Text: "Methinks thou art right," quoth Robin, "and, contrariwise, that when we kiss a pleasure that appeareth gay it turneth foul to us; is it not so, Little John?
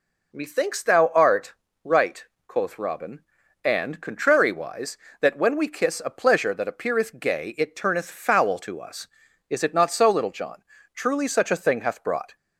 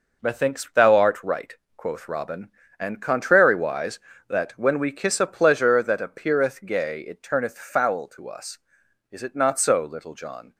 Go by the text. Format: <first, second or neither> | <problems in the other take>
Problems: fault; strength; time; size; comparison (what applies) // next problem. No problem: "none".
second | pauses between "art" and "right"; slight; at 1.5 s; 0.32 s long // goes on to say "Truly such a thing hath brought"; from 10.9 s on; 1.4 s long